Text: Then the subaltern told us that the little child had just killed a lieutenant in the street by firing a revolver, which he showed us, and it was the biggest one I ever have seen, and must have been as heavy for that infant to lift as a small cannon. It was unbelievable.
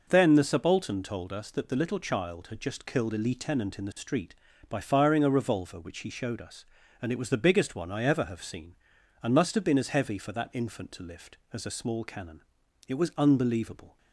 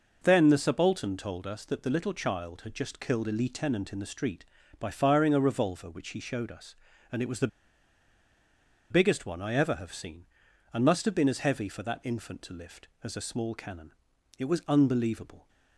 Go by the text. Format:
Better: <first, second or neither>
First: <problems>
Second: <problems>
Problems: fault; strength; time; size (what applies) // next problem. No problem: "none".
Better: first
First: none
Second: pauses between "the" and "biggest"; strong; at 7.4 s; 1.4 s long